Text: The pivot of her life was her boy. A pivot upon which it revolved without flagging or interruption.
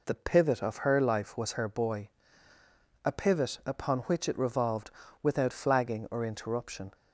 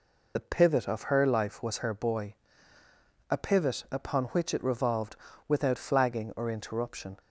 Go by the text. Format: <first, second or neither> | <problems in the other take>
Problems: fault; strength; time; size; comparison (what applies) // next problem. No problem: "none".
first | loses the start of "The"; at 0.3 s; 35 ms // pauses between "revolved" and "without"; slight; at 5.1 s; 0.32 s long; slight in the first